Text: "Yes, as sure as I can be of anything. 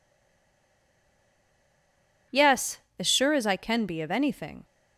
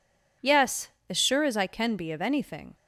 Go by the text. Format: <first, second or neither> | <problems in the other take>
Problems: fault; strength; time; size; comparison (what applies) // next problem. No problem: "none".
second | stays silent before the first word; until 2.3 s; 2.3 s long